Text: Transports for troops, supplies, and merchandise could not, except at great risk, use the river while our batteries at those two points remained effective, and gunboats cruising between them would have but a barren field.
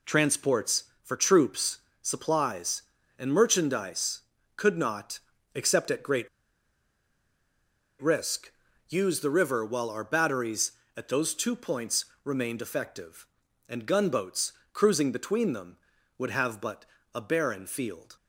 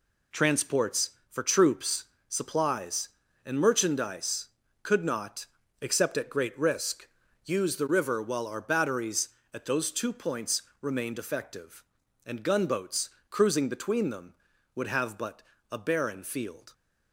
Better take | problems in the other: second | pauses between "great" and "risk"; strong; at 6.2 s; 1.7 s long // pauses between "points" and "remained"; slight; at 12.0 s; 0.18 s long; slight in the second // pauses between "gunboats" and "cruising"; slight; at 14.5 s; 0.18 s long; slight in the second // pauses between "but" and "a"; slight; at 16.8 s; 0.28 s long; slight in the second

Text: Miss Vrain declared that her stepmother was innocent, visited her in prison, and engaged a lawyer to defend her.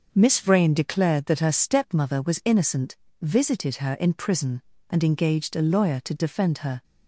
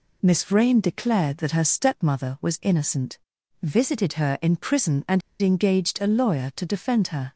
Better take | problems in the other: first | pauses between "and" and "engaged"; slight; at 5.2 s; 0.21 s long

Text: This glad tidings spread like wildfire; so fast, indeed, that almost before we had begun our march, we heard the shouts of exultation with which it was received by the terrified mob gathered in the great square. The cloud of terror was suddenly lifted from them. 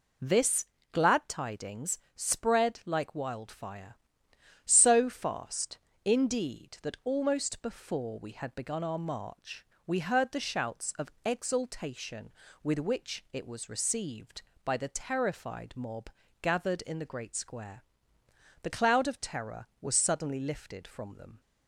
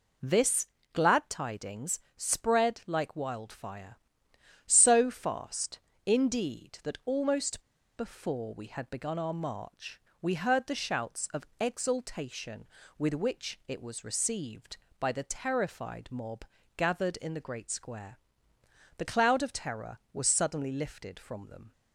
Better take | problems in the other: first | pauses between "This" and "glad"; slight; at 0.6 s; 0.26 s long; slight in the first // pauses between "tidings" and "spread"; slight; at 1.9 s; 0.16 s long; slight in the first // pauses between "almost" and "before"; slight; at 7.6 s; 0.34 s long // pauses between "mob" and "gathered"; slight; at 16.4 s; 0.32 s long; slight in the first

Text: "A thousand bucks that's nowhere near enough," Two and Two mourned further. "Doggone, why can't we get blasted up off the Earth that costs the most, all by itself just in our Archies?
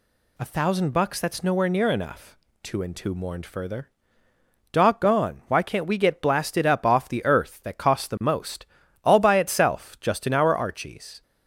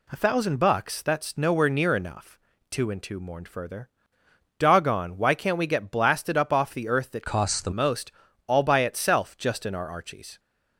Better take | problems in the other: first | changes voice from "costs" to "the"; from 7.2 to 7.6 s; 0.4 s long

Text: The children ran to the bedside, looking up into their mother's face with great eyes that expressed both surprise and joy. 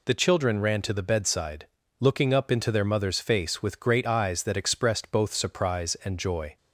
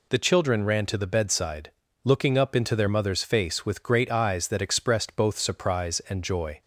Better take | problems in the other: neither | none

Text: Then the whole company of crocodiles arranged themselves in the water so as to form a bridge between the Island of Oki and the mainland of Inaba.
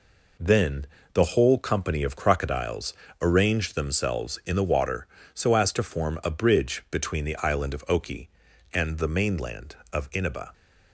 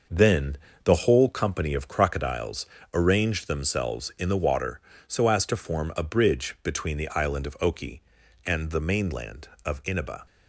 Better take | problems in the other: first | starts louder than the rest; noticeable; until 1.4 s; 6 dB // pauses between "Then" and "the"; slight; at 0.5 s; 0.28 s long; slight in the first // pauses between "crocodiles" and "arranged"; slight; at 2.6 s; 0.26 s long; slight in the first

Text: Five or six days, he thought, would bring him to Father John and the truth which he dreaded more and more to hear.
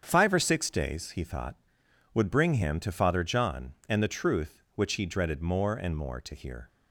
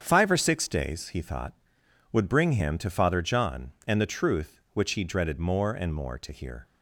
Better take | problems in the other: neither | starts louder than the rest; strong; the same in both

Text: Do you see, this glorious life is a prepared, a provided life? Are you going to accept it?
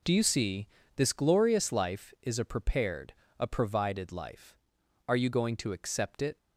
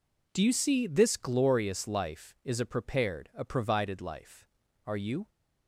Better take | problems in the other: first | stops before "going to accept it"; at 5.2 s

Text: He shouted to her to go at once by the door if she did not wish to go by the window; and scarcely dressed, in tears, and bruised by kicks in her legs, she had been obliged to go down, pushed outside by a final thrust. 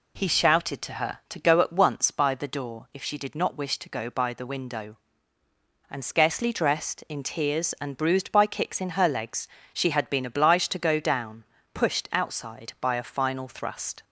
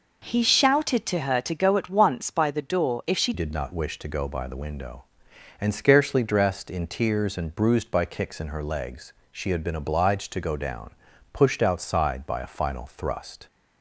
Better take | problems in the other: first | changes voice at "did"; from 3.3 s on; 10.1 s long

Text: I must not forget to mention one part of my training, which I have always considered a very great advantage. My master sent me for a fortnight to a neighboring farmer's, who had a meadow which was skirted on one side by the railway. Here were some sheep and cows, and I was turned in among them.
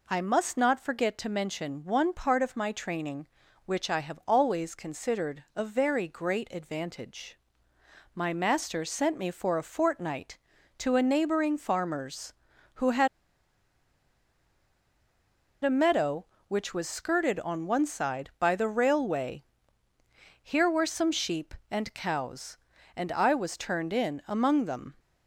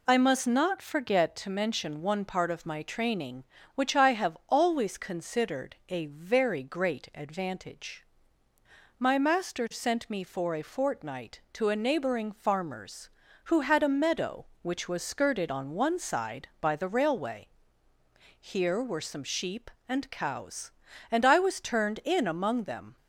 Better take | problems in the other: second | pauses between "had" and "a"; strong; at 13.0 s; 2.5 s long

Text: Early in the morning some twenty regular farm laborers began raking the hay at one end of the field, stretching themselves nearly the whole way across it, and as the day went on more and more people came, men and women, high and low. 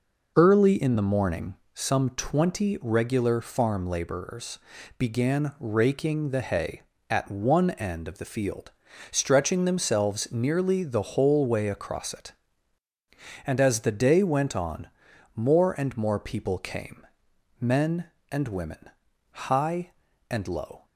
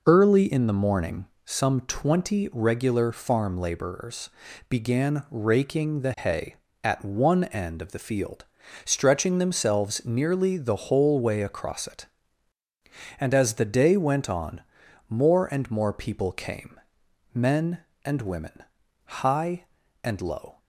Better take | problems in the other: neither | pauses between "morning" and "some"; slight; the same in both // pauses between "laborers" and "began"; the same in both // pauses between "on" and "more"; noticeable; the same in both

